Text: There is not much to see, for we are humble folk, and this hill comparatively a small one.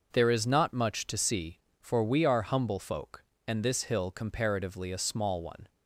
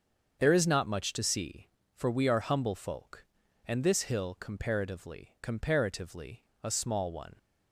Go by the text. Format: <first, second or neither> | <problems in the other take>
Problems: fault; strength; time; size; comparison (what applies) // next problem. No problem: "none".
first | starts louder than the rest; until 1.4 s; 7 dB // says "comparatively" twice; at 5.4 s